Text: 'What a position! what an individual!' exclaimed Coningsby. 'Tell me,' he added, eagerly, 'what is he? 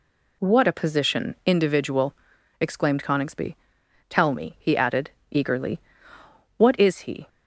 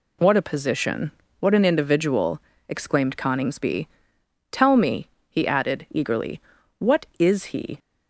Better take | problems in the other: second | skips "what an"; at 1.4 s

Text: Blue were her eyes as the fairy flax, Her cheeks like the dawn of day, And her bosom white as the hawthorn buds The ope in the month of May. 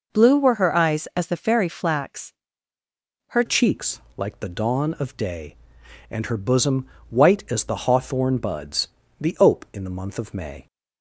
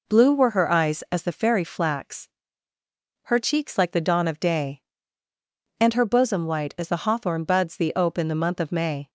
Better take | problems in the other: second | changes voice at "cheeks"; from 3.4 s on; 7.2 s long // pauses between "cheeks" and "like"; slight; at 3.9 s; 0.18 s long // pauses between "bosom" and "white"; slight; at 6.8 s; 0.22 s long // pauses between "buds" and "The"; slight; at 8.8 s; 0.32 s long

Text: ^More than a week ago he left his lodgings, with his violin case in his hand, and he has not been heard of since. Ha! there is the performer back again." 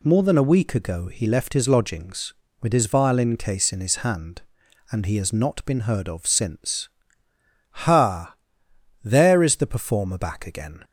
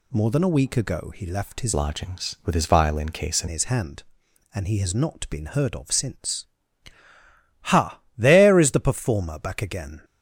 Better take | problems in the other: first | changes voice from "lodgings" to "in"; from 1.7 to 3.4 s; 1.7 s long

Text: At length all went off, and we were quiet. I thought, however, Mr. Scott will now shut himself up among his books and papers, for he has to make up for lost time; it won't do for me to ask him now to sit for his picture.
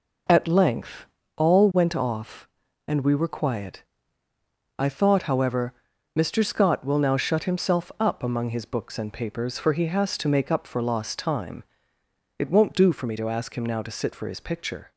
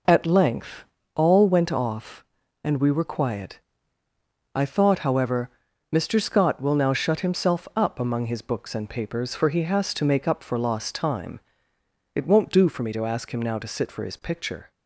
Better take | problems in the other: neither | pauses between "length" and "all"; slight; the same in both

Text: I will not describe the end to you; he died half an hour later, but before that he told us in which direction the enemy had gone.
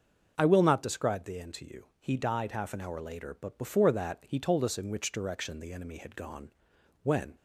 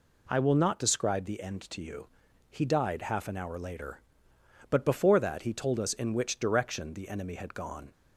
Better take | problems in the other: second | starts louder than the rest; noticeable; until 1.3 s; 6 dB // goes on to say "When"; slight; from 7.0 s on; 0.32 s long

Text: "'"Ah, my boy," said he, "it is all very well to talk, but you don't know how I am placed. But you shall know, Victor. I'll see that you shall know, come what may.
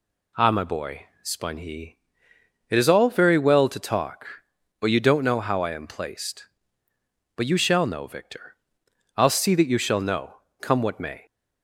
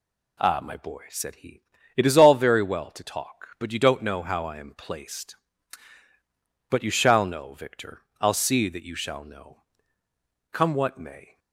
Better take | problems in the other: second | says "spun" for "said"; at 1.2 s

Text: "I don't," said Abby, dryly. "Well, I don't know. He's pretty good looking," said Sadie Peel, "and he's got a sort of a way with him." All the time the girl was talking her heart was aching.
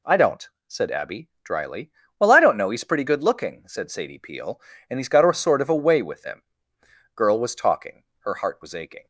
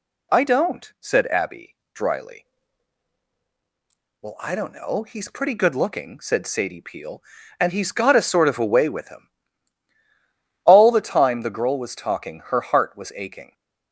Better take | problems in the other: second | skips "All the time the"; at 6.7 s // pauses between "talking" and "her"; slight; at 8.0 s; 0.16 s long

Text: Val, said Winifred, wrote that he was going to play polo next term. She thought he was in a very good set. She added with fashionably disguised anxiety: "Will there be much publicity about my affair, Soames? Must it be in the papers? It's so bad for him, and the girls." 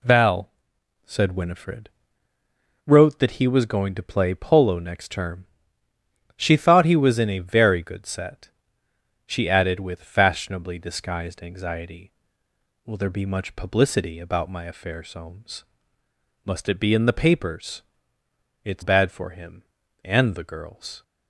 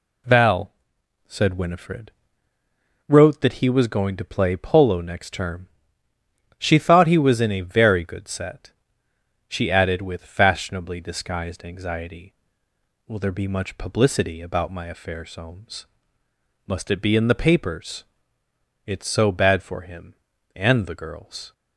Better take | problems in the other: second | skips "so"; at 18.8 s

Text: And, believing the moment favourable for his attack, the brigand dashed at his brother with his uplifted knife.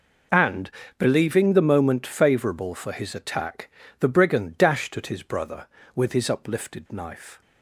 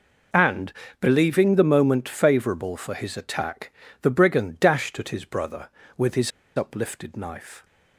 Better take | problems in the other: first | pauses between "his" and "uplifted"; slight; at 6.3 s; 0.26 s long

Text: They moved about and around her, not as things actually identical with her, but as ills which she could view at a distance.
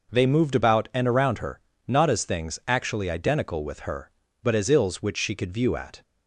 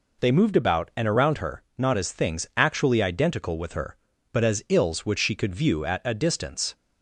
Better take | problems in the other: second | stops before "a distance"; at 6.0 s

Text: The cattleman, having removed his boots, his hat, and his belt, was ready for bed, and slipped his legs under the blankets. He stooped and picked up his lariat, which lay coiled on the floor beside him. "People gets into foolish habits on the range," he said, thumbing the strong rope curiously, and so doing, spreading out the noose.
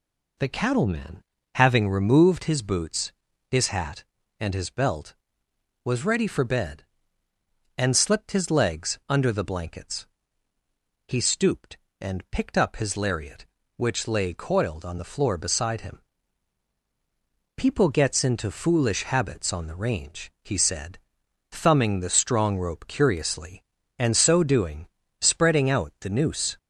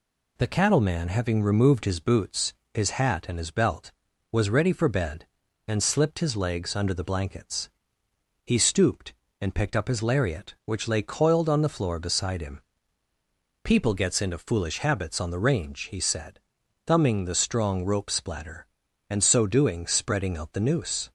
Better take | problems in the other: first | says "splatter" for "curiously"; at 18.1 s

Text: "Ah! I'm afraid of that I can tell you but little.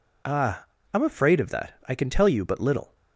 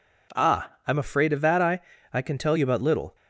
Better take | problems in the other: first | says "I" twice; at 2.1 s

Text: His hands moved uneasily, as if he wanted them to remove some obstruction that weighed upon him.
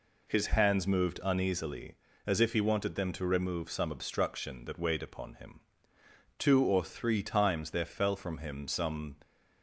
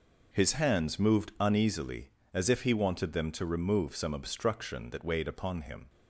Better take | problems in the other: second | goes on to say "Two or three times there fell from him some"; strong; from 6.3 s on; 2.8 s long

